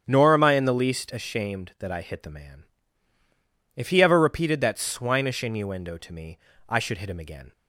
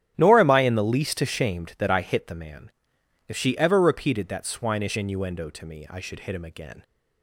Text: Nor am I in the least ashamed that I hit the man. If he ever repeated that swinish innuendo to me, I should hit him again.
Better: first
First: starts louder than the rest; strong; until 1.0 s; 8.5 dB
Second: starts louder than the rest; strong; until 1.1 s; 11 dB // says "she" for "he"; at 3.3 s

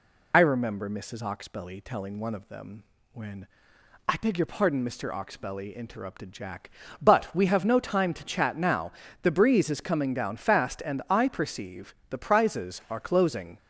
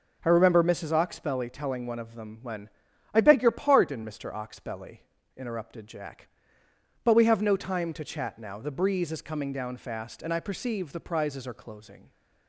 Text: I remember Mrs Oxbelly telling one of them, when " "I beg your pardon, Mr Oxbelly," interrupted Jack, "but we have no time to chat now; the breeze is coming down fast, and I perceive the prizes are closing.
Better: second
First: loses the start of "I"; at 0.3 s; 50 ms // pauses between "perceive" and "the"; slight; at 11.9 s; 0.16 s long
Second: none

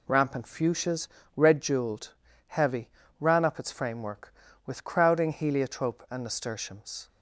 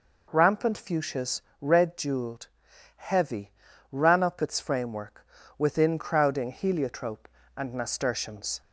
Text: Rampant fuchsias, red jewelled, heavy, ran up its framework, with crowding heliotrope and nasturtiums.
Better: first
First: none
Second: says "within" for "with"; at 5.5 s

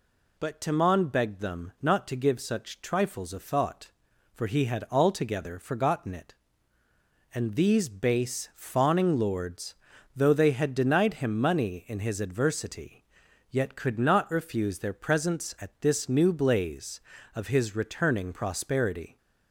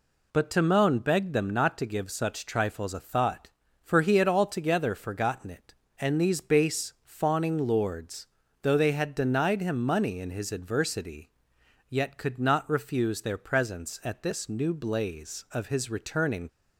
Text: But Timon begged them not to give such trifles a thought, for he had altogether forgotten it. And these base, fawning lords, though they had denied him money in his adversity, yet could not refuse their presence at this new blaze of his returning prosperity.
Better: first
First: none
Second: stops before "prosperity"; at 16.4 s

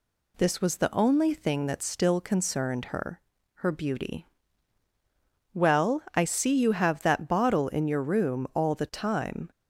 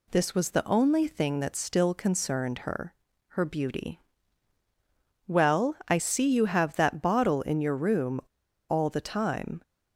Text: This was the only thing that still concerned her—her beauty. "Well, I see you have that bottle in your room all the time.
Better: first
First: none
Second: pauses between "room" and "all"; noticeable; at 8.2 s; 0.46 s long

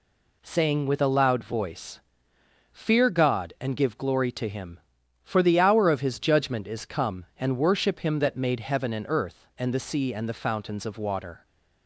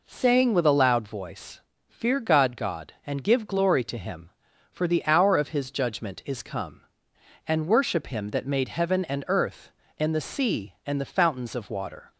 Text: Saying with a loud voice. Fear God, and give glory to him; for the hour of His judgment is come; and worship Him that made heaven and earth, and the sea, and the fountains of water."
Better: first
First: none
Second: says "God" twice; at 2.5 s

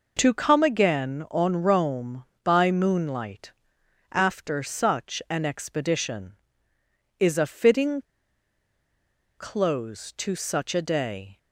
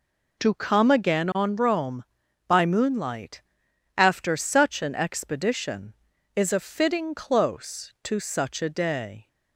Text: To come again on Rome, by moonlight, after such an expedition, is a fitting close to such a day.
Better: second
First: pauses between "fitting" and "close"; strong; at 8.0 s; 1.3 s long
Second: none

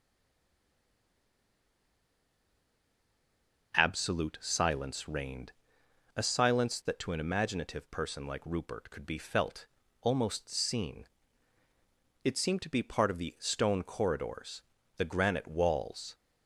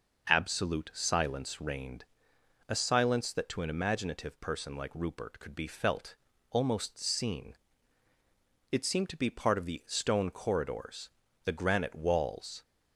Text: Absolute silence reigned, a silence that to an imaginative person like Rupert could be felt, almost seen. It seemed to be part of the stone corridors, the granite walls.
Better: second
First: stays silent before the first word; strong; until 3.7 s; 3.7 s long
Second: none

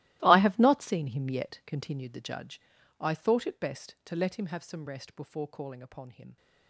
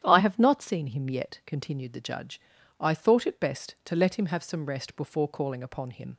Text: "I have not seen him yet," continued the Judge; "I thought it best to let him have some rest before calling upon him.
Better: second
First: gets quieter; strong; throughout; 16.5 dB // starts louder than the rest; strong; until 1.2 s; 17 dB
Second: starts louder than the rest; strong; until 1.0 s; 10.5 dB

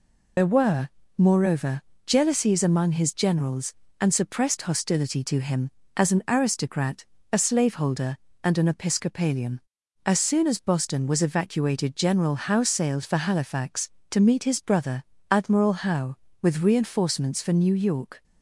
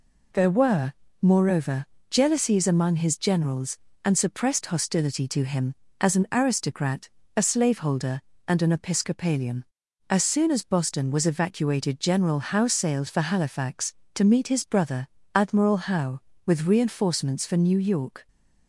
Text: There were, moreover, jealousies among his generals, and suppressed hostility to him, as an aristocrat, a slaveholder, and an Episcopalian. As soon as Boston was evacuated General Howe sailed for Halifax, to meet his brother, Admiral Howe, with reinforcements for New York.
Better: second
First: loses the start of "There"; at 0.3 s; 80 ms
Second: none

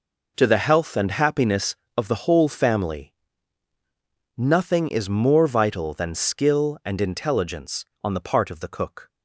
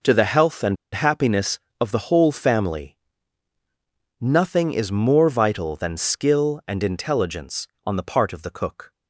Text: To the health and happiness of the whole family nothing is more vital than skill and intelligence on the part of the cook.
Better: first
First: pauses between "family" and "nothing"; at 3.1 s; 1.2 s long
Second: pauses between "and" and "happiness"; slight; at 0.7 s; 0.18 s long // pauses between "family" and "nothing"; at 2.9 s; 1.2 s long

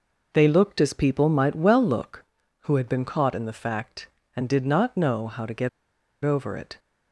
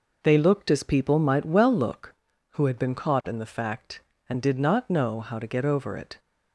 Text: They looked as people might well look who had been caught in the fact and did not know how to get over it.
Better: second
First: pauses between "get" and "over"; noticeable; at 5.6 s; 0.55 s long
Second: none

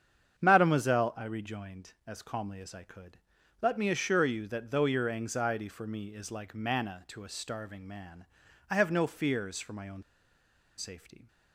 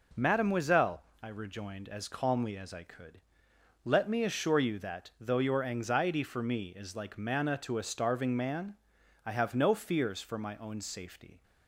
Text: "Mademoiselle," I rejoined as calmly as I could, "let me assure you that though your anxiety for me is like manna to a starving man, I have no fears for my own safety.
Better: second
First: starts louder than the rest; strong; until 1.4 s; 8 dB // pauses between "own" and "safety"; noticeable; at 10.0 s; 0.74 s long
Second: none

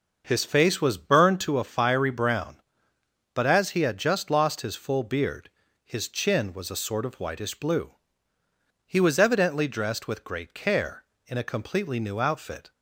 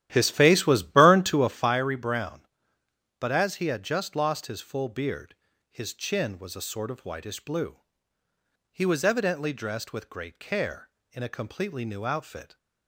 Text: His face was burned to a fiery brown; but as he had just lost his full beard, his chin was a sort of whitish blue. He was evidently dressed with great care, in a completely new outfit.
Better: first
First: none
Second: starts louder than the rest; strong; until 1.8 s; 12.5 dB

